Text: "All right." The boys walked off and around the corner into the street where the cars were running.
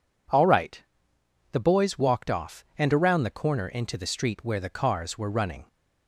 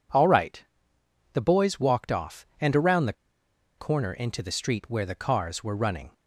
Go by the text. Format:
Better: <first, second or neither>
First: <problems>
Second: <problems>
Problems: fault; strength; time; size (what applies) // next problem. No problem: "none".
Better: first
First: none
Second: pauses between "the" and "corner"; noticeable; at 3.1 s; 0.65 s long